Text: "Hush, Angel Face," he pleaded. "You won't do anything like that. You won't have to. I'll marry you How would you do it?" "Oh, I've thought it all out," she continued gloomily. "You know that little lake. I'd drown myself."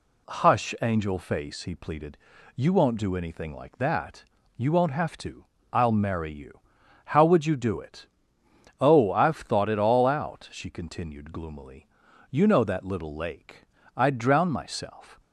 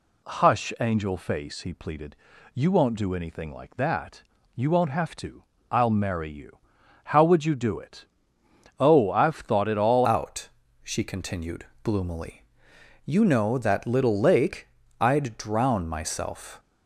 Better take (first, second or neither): first